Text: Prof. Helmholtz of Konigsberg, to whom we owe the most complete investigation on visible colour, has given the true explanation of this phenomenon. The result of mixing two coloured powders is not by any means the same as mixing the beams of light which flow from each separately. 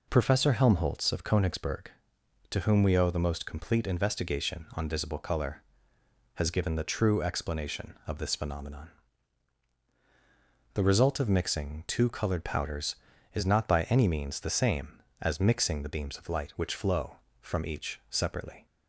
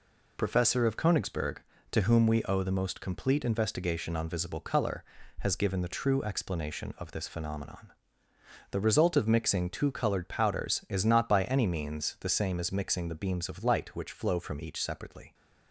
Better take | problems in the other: first | skips "Helmholtz"; at 0.8 s

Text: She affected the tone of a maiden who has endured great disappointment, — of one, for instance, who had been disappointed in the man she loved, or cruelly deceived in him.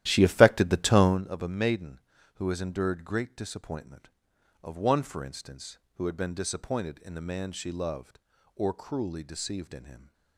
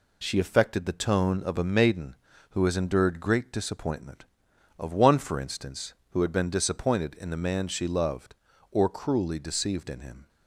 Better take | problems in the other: second | starts louder than the rest; strong; until 1.2 s; 13 dB

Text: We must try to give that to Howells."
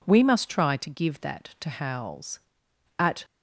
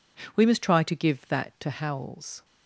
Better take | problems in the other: second | goes on to say "At"; slight; from 2.9 s on; 0.26 s long

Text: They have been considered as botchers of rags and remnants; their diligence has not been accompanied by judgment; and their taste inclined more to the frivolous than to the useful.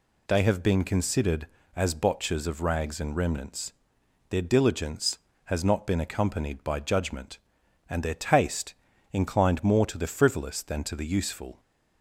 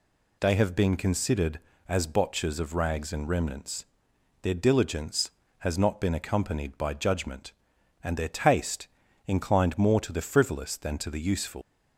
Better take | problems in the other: first | pauses between "taste" and "inclined"; at 8.8 s; 0.40 s long; also in the first // leaves "useful" unfinished; at 11.6 s; 130 ms

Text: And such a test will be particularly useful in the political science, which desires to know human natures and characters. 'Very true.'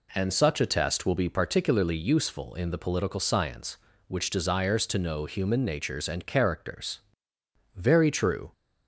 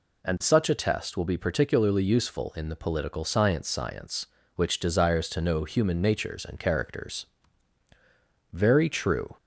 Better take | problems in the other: first | says "science" twice; at 3.6 s

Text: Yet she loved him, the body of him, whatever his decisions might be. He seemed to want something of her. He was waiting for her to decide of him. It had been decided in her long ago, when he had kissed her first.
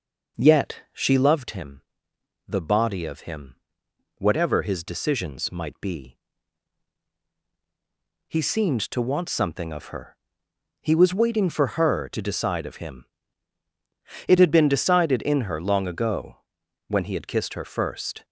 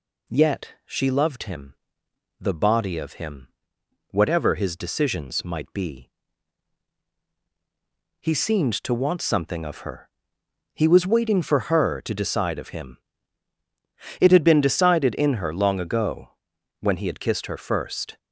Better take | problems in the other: second | starts louder than the rest; noticeable; until 1.5 s; 5.5 dB

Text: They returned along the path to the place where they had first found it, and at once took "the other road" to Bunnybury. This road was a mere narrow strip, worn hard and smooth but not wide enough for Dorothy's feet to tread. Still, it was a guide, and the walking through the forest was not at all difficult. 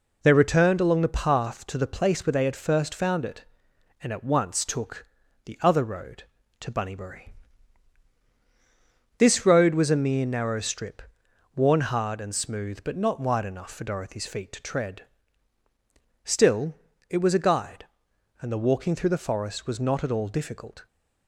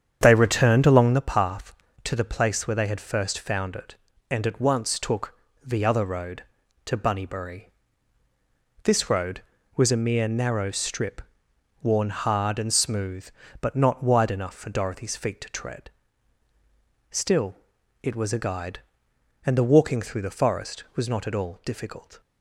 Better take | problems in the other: first | starts louder than the rest; strong; until 1.3 s; 8.5 dB // pauses between "took" and "the"; slight; at 5.3 s; 0.32 s long; also in the first

